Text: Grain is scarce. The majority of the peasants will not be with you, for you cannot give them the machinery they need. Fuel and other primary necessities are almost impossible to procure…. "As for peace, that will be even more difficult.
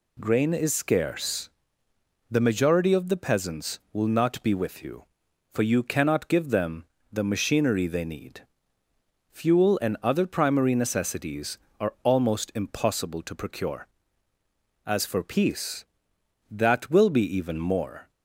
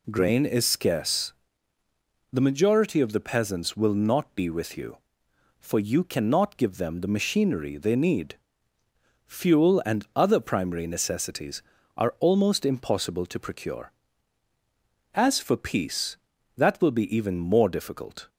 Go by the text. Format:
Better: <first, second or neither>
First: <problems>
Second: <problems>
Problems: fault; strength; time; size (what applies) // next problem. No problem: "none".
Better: second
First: pauses between "them" and "the"; slight; at 6.8 s; 0.26 s long // stops before "difficult"; at 18.1 s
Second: none